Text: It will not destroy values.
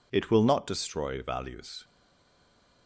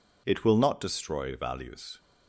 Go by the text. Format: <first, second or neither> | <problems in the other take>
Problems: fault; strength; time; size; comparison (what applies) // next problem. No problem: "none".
second | stays silent after the last word; from 1.8 s on; 1.0 s long